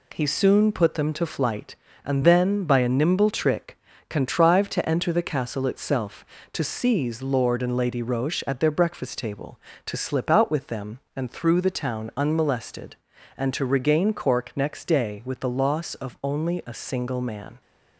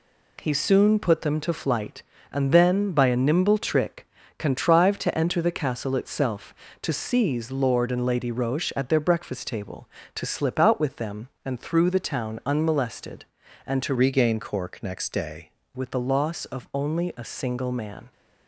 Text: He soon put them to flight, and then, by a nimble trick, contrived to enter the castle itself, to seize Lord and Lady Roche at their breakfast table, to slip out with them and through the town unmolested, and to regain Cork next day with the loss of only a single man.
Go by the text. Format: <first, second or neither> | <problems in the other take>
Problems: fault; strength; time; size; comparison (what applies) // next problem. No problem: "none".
first | changes voice from "regain" to "day"; from 13.9 to 15.5 s; 1.6 s long